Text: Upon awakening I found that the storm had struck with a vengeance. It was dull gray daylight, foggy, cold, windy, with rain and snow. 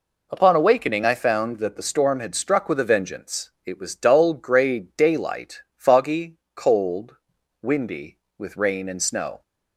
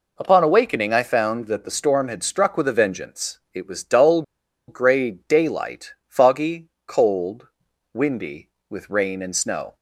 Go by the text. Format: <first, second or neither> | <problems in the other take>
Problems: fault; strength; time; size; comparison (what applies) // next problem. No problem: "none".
first | pauses between "dull" and "gray"; at 4.2 s; 0.45 s long